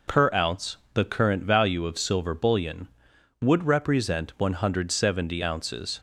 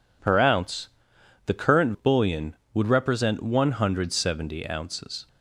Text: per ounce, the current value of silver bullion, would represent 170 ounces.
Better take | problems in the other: first | skips "value of silver"; at 1.9 s

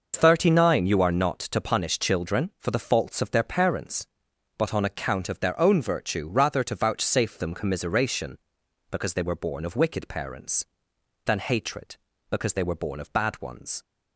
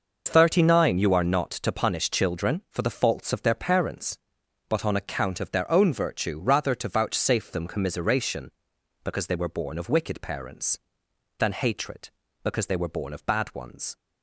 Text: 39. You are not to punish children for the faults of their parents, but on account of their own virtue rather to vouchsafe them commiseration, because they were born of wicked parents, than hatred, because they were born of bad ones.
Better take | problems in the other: neither | none

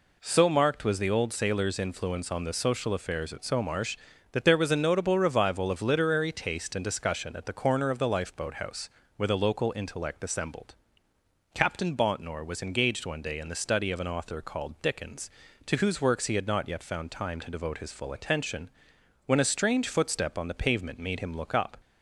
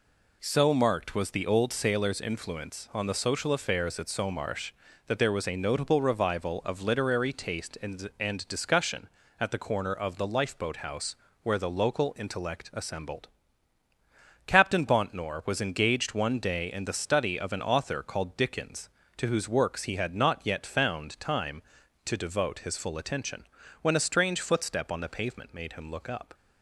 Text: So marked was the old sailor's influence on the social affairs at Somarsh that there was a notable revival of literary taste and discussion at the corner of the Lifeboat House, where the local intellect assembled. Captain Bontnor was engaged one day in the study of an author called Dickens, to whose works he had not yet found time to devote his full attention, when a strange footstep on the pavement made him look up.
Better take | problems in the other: first | says "and" twice; at 8.1 s

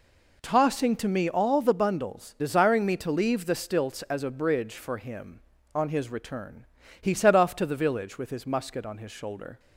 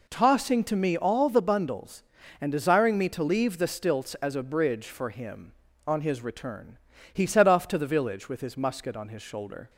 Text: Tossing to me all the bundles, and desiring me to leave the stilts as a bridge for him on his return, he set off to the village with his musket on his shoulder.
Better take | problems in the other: second | skips "and"; at 2.3 s

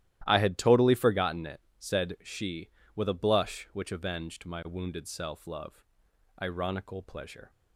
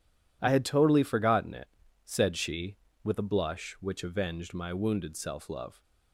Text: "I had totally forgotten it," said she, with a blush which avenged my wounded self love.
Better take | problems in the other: second | starts louder than the rest; strong; until 1.2 s; 13.5 dB // goes on to say "Ironical pleasure"; noticeable; from 6.4 s on; 1.1 s long

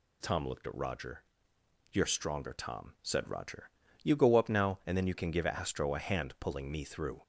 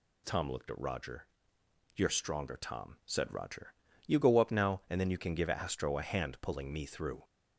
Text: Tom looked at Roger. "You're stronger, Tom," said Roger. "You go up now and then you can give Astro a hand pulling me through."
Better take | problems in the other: neither | none

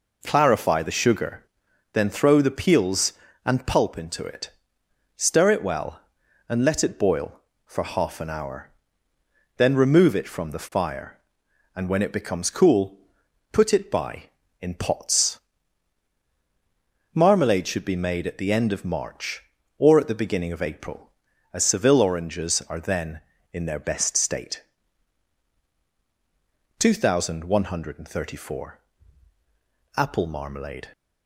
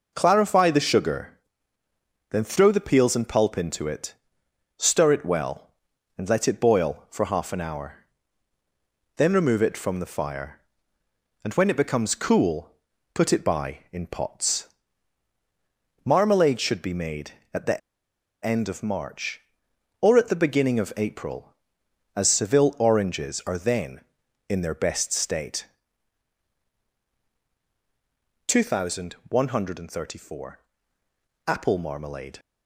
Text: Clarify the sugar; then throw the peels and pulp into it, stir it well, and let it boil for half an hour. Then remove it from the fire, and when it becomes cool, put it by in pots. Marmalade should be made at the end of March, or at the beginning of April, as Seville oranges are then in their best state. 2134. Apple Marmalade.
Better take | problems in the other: first | pauses between "the" and "end"; noticeable; at 17.7 s; 0.65 s long

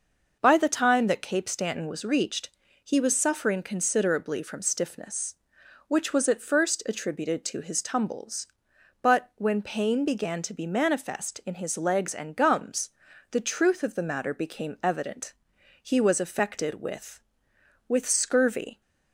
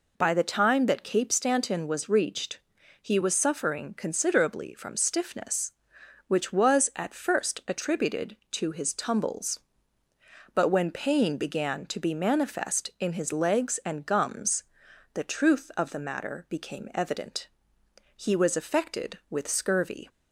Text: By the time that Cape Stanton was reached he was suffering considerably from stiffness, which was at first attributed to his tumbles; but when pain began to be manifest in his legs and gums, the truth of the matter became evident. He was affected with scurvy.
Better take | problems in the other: second | pauses between "reached" and "he"; slight; at 2.5 s; 0.33 s long; also in the second // says "with" twice; at 17.8 s

